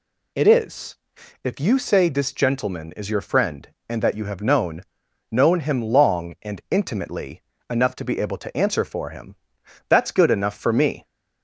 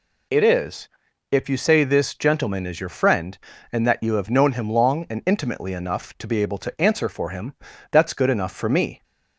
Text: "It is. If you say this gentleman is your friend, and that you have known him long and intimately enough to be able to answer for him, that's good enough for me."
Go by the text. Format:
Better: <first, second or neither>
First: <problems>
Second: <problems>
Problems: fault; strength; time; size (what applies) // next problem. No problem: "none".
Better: second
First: says "known" twice; at 5.2 s // pauses between "intimately" and "enough"; slight; at 7.4 s; 0.28 s long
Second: none